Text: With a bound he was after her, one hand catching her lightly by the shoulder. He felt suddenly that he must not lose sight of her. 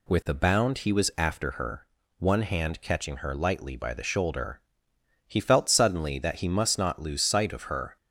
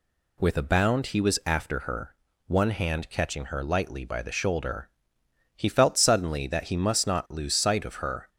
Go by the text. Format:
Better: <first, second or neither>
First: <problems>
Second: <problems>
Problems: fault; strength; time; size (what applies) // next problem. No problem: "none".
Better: neither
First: none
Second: none